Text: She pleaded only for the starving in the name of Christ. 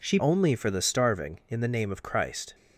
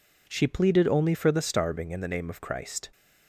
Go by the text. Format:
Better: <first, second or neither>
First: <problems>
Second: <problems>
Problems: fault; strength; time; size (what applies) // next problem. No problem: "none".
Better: second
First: skips "pleaded"; at 0.1 s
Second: none